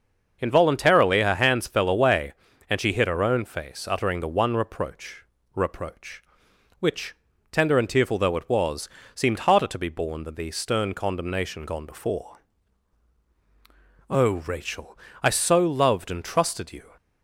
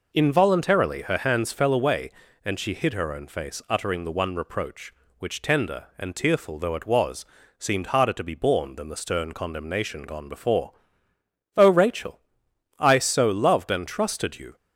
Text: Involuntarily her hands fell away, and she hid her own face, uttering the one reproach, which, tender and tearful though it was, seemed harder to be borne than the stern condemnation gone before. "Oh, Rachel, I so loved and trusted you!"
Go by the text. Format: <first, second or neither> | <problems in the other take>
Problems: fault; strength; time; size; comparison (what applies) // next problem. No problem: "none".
second | starts louder than the rest; until 1.4 s; 6.5 dB // says "reproach" twice; at 5.5 s